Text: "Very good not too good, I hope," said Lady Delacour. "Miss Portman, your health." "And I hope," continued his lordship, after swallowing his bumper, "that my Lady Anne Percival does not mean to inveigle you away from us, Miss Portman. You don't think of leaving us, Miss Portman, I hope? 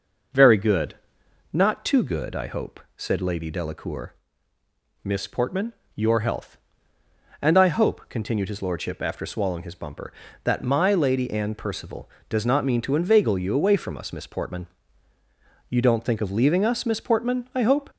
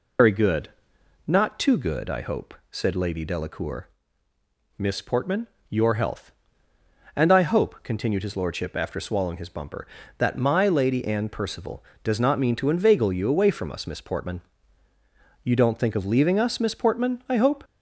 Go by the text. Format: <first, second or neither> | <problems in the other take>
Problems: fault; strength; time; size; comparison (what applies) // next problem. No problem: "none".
first | loses the start of "Very"; at 0.1 s; 115 ms // pauses between "good" and "not"; noticeable; at 0.6 s; 0.56 s long; noticeable in the first